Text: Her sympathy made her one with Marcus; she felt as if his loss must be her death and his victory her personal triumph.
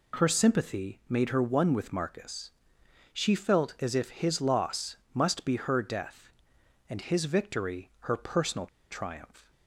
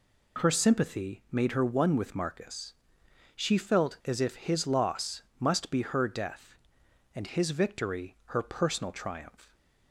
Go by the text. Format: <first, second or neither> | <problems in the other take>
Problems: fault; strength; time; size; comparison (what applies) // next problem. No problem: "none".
second | pauses between "loss" and "must"; slight; at 4.9 s; 0.18 s long; slight in the second // pauses between "personal" and "triumph"; slight; at 8.6 s; 0.24 s long